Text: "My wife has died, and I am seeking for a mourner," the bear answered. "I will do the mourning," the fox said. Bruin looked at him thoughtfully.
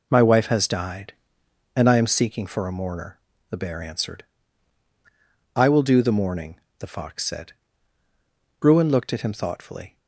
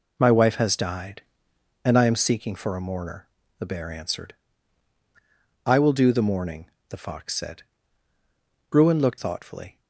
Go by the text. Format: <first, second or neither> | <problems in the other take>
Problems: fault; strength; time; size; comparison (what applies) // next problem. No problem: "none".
first | skips "at him"; at 9.1 s